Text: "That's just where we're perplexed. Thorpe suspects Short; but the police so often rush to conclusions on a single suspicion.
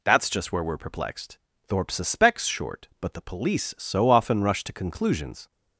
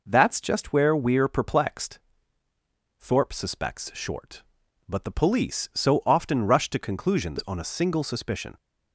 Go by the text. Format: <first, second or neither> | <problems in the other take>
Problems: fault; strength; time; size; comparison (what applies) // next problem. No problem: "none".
second | stops before "on a single suspicion"; at 5.5 s